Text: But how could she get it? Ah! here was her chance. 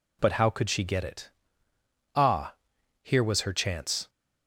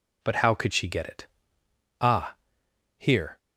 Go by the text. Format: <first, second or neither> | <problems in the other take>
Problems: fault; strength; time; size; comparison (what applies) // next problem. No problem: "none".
first | stops before "was her chance"; at 3.3 s